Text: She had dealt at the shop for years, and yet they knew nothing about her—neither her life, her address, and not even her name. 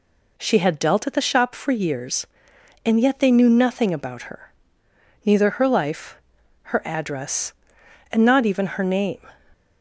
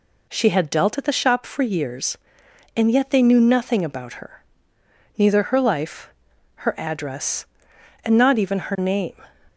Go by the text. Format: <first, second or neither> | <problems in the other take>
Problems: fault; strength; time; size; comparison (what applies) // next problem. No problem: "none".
neither | none